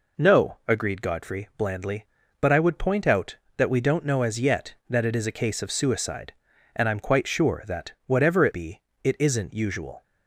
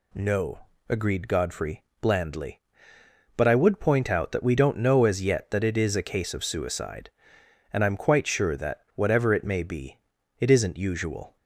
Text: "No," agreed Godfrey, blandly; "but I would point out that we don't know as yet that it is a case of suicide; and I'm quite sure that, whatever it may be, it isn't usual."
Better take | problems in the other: second | skips "may"; at 8.5 s

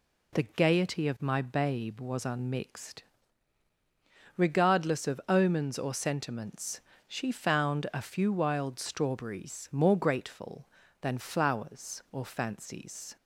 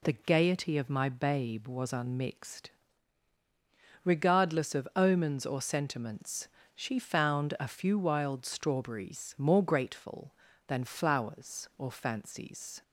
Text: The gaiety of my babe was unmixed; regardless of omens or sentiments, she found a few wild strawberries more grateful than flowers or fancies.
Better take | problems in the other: neither | none

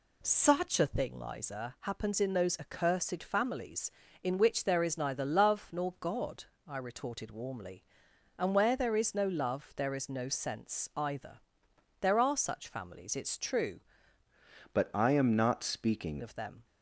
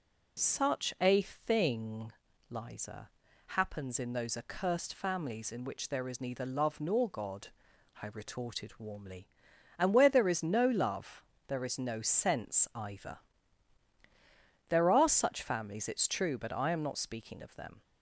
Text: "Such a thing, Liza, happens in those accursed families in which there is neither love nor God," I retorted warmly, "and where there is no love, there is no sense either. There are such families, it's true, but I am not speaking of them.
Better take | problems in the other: second | changes voice from "but" to "speaking"; from 14.7 to 16.1 s; 1.4 s long

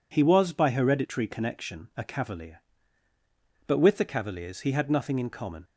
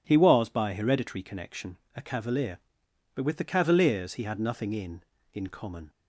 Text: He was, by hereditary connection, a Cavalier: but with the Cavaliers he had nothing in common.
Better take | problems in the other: first | says "in" twice; at 5.3 s

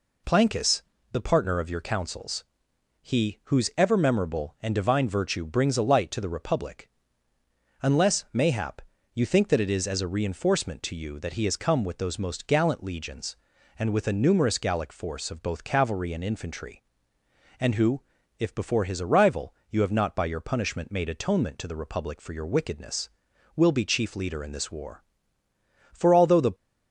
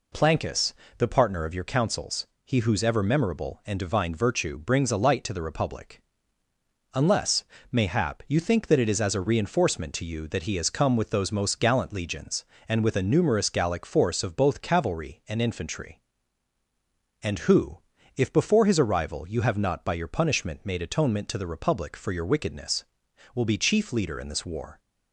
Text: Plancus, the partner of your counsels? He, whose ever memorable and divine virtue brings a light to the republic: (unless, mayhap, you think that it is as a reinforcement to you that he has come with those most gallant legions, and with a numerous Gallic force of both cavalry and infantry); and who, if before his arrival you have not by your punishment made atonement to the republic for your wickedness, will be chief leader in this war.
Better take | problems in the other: second | goes on to say "For although the"; noticeable; from 25.9 s on; 0.62 s long

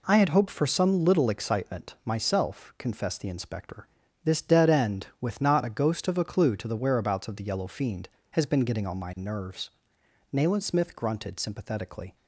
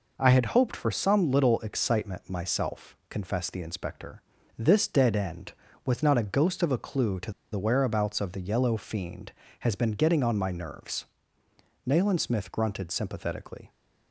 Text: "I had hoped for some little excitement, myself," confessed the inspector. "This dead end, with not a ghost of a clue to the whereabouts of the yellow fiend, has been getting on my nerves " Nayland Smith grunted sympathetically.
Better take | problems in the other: first | pauses between "to" and "the"; slight; at 7.3 s; 0.20 s long

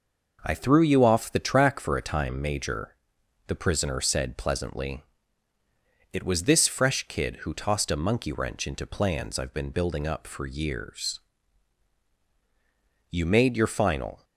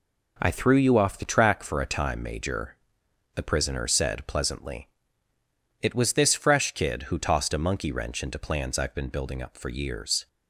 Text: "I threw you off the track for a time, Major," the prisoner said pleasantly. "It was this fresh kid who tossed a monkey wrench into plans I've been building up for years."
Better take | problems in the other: second | goes on to say "You made your final"; noticeable; from 13.0 s on; 1.1 s long

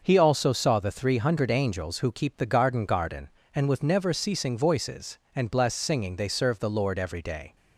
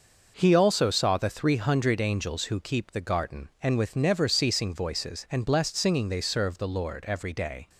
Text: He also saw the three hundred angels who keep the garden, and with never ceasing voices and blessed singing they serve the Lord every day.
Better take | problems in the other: second | starts louder than the rest; noticeable; until 1.0 s; 6 dB // says "garden" twice; at 2.8 s

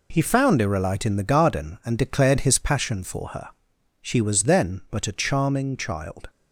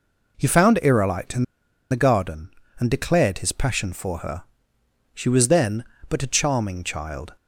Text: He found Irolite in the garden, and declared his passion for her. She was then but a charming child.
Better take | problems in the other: first | pauses between "in" and "the"; noticeable; at 1.4 s; 0.46 s long

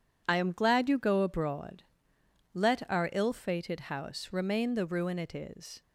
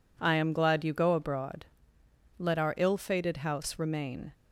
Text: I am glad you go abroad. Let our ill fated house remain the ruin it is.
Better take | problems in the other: first | stops before "the ruin it is"; at 4.3 s

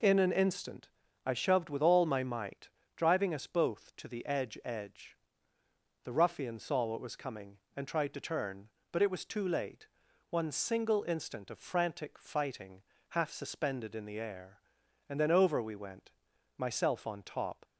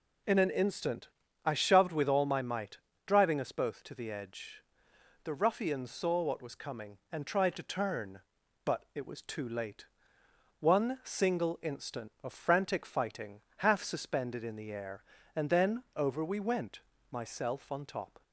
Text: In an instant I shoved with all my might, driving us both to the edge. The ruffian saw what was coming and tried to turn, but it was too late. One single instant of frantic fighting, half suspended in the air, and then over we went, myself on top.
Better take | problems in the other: second | pauses between "instant" and "I"; at 0.8 s; 0.40 s long; slight in the second // says "edge" twice; at 4.6 s

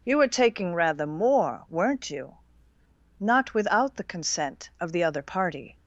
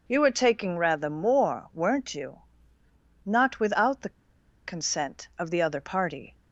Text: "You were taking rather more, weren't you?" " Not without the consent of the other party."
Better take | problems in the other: first | pauses between "the" and "consent"; noticeable; at 4.1 s; 0.55 s long

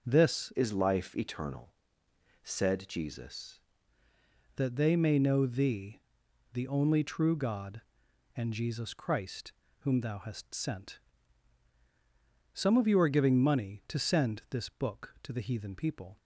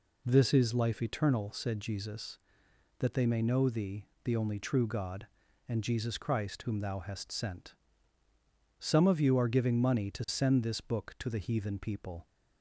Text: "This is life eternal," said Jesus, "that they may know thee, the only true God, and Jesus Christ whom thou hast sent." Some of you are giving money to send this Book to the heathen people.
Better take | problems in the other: second | changes voice from "is" to "Jesus"; from 0.5 to 3.5 s; 3.0 s long // pauses between "Christ" and "whom"; slight; at 9.5 s; 0.28 s long

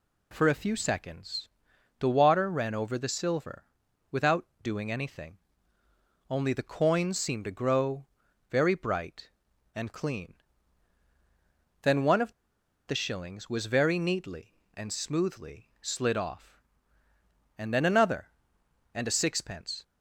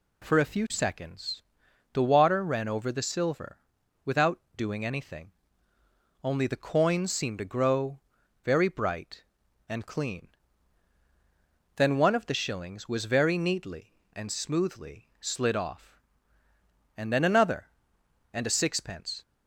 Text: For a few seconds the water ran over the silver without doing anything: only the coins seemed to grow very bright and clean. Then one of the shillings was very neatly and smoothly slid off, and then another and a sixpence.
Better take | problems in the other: second | pauses between "seconds" and "the"; noticeable; at 1.4 s; 0.50 s long; noticeable in the second // pauses between "silver" and "without"; at 3.6 s; 0.44 s long; also in the second // pauses between "without" and "doing"; slight; at 4.4 s; 0.16 s long; slight in the second // pauses between "grow" and "very"; at 8.0 s; 0.44 s long; also in the second // pauses between "of" and "the"; noticeable; at 12.3 s; 0.55 s long

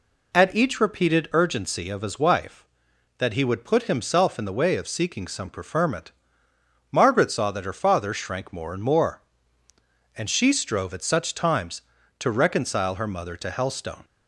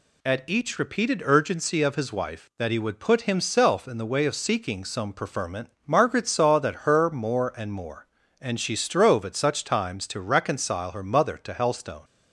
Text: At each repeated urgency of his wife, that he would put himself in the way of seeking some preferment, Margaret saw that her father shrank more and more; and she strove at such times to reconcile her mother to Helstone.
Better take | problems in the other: first | skips "father shrank"; at 7.0 s

